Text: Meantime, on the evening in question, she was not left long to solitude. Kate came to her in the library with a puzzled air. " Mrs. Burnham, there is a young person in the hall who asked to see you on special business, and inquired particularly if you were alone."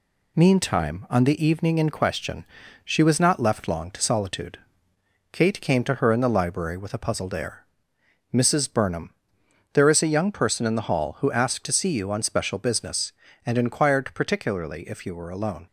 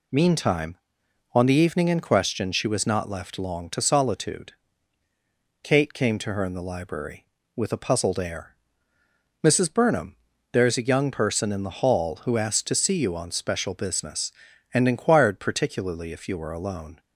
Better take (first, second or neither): neither